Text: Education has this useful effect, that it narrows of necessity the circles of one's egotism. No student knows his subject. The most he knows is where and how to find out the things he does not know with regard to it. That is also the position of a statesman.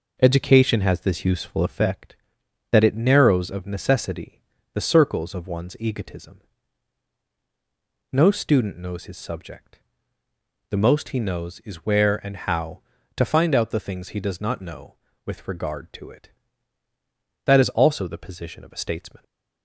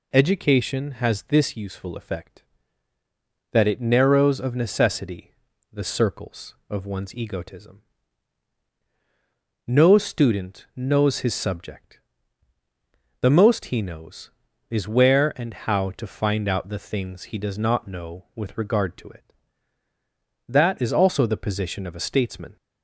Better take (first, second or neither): second